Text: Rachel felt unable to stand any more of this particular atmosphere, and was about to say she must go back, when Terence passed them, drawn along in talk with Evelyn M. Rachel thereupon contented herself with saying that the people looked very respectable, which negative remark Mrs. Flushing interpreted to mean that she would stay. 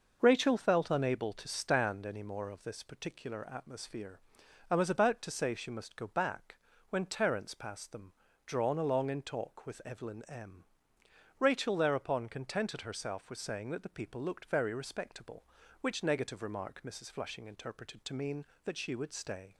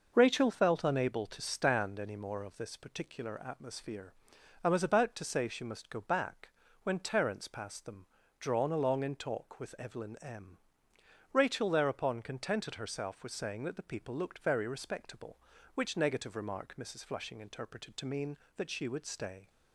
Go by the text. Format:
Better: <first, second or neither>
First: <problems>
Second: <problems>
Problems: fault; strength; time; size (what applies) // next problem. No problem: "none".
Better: neither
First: none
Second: none